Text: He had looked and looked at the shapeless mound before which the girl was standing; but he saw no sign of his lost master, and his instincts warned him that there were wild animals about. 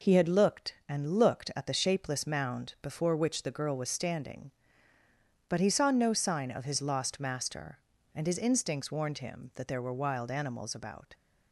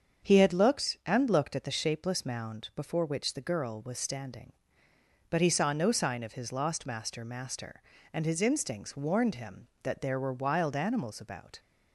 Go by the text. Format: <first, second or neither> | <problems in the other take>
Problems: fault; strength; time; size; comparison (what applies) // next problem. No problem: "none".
first | starts louder than the rest; until 1.3 s; 7 dB // says "master" twice; at 7.2 s